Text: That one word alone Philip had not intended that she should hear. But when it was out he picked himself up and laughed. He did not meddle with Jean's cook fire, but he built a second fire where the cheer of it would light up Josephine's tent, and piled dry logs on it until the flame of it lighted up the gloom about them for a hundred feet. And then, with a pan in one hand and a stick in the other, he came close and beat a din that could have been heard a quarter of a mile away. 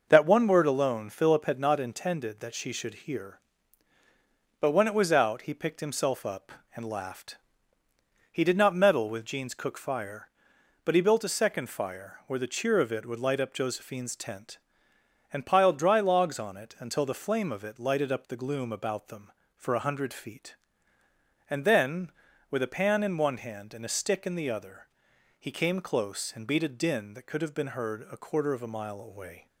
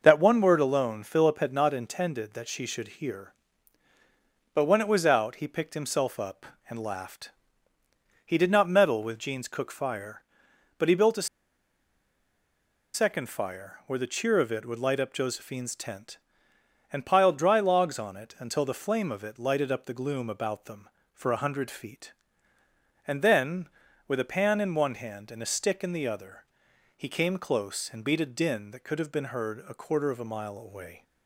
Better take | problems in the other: first | pauses between "a" and "second"; strong; at 11.2 s; 1.6 s long

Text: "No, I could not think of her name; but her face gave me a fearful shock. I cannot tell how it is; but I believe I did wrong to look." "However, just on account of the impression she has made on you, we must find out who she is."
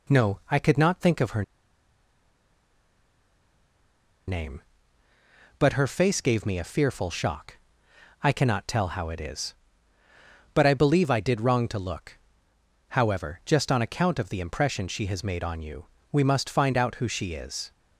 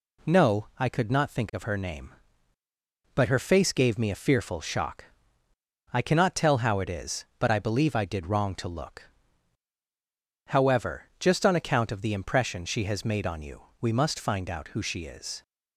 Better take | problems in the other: second | pauses between "her" and "name"; strong; at 1.4 s; 2.8 s long

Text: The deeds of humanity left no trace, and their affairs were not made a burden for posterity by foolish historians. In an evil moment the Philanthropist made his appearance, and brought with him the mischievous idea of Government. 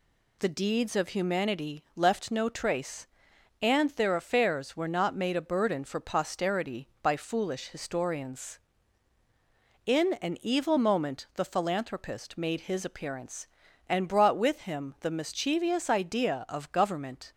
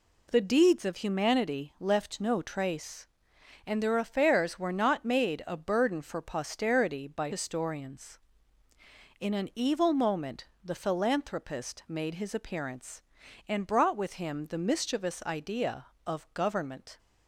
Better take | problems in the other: first | skips "foolish"; at 7.3 s // pauses between "moment" and "the"; slight; at 10.4 s; 0.18 s long

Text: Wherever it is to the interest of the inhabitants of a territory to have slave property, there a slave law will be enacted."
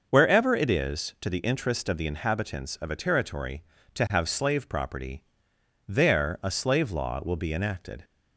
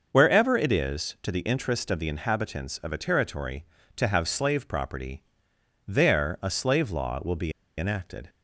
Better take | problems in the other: first | starts louder than the rest; noticeable; until 1.1 s; 6 dB; noticeable in the first // pauses between "be" and "enacted"; slight; at 7.5 s; 0.26 s long

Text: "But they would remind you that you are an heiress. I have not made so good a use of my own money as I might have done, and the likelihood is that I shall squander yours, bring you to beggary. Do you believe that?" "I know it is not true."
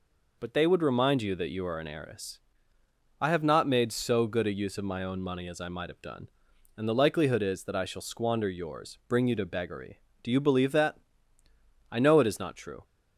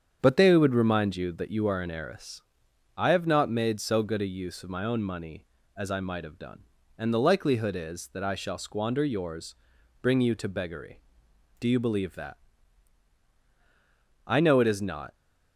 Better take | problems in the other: first | starts louder than the rest; strong; until 1.2 s; 7.5 dB // stops before "true"; at 15.1 s

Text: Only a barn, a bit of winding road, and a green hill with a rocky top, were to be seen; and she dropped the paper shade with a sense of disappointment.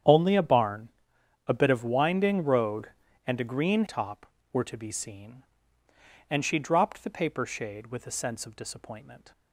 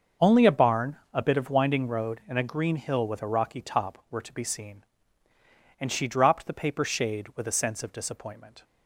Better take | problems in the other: second | starts louder than the rest; strong; until 1.6 s; 9 dB; also in the second // skips "hill with a rocky"; at 3.8 s

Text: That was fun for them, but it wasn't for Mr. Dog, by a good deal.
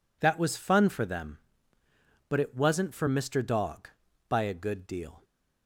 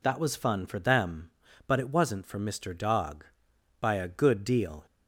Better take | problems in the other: neither | none

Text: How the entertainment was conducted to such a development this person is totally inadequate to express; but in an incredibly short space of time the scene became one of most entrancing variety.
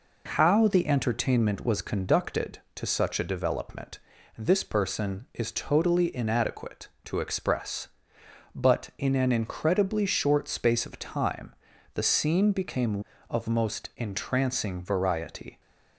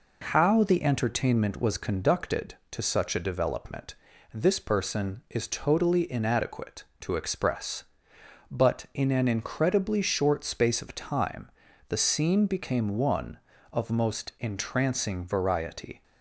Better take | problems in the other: second | pauses between "development" and "this"; slight; at 4.0 s; 0.36 s long; slight in the second // pauses between "time" and "the"; at 11.5 s; 0.40 s long; also in the second // skips "one"; at 13.1 s

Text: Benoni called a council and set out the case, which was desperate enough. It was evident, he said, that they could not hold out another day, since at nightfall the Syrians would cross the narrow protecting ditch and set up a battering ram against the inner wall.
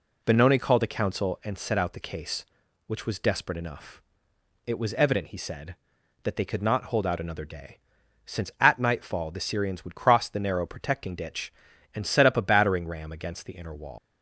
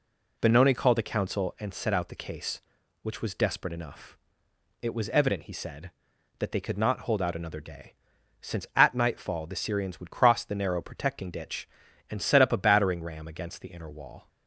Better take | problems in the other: second | leaves "wall" unfinished; at 13.9 s; 140 ms

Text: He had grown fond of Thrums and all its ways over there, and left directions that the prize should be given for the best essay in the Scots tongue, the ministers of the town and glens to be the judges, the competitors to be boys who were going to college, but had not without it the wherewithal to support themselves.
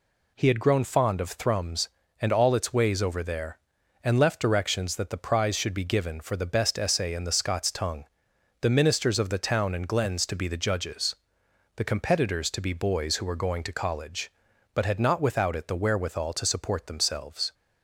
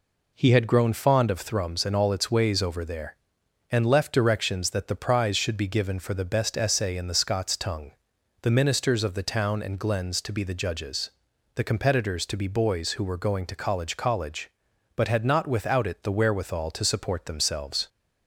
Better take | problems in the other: first | says "college" twice; at 13.9 s

